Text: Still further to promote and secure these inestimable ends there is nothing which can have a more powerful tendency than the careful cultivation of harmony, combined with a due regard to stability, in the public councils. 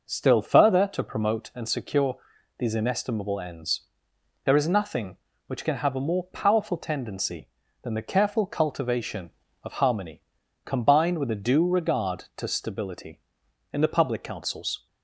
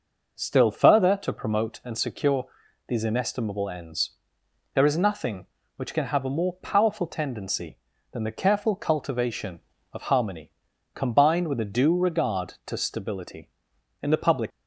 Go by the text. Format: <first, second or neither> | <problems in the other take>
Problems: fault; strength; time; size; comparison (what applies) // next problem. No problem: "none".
first | pauses between "secure" and "these"; at 2.4 s; 0.42 s long; also in the first // pauses between "ends" and "there"; noticeable; at 4.1 s; 0.62 s long; noticeable in the first // stops before "councils"; at 14.5 s